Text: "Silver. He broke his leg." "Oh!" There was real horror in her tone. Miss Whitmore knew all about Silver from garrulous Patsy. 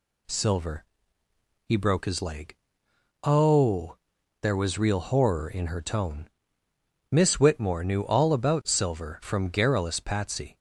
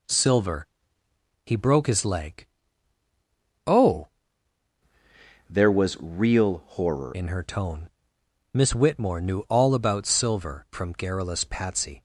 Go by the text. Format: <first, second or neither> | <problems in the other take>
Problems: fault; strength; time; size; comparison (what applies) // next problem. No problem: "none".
first | changes voice from "There" to "horror"; from 5.4 to 7.1 s; 1.7 s long